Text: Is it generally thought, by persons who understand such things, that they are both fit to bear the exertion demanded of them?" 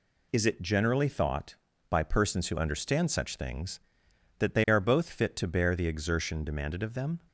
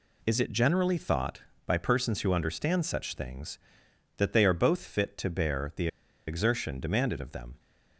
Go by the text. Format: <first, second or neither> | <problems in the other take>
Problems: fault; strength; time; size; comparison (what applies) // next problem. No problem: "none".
first | pauses between "the" and "exertion"; at 5.8 s; 0.40 s long